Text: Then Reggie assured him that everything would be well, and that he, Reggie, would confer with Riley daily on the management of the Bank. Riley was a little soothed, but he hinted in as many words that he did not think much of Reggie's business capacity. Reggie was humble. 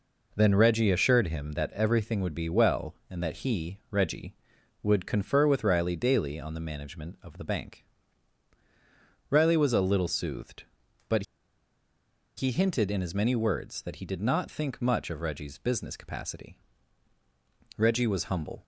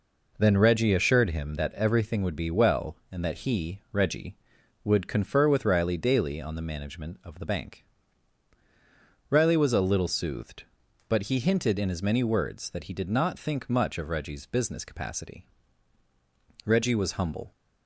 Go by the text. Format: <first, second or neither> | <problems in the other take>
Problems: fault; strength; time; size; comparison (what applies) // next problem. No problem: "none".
second | pauses between "but" and "he"; at 11.2 s; 1.1 s long